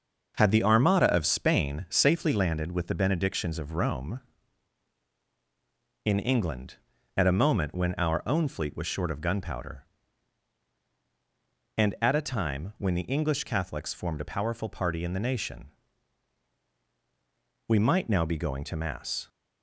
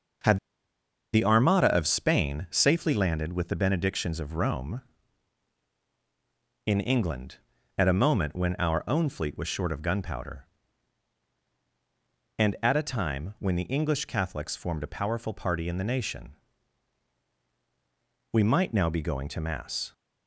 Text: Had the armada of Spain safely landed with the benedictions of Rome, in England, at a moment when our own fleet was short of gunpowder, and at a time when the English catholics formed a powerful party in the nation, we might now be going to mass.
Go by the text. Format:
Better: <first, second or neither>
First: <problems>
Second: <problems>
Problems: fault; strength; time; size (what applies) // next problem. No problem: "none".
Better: first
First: starts louder than the rest; until 1.3 s; 6.5 dB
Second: starts louder than the rest; until 1.9 s; 6.5 dB // pauses between "Had" and "the"; noticeable; at 0.3 s; 0.75 s long